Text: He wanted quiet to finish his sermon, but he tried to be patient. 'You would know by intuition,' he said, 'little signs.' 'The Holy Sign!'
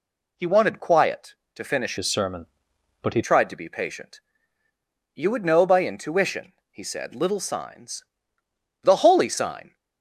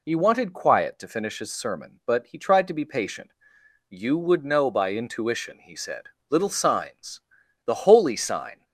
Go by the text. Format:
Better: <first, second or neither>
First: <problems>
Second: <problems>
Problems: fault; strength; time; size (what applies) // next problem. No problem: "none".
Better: second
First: changes voice from "his" to "he"; from 1.9 to 3.2 s; 1.3 s long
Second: none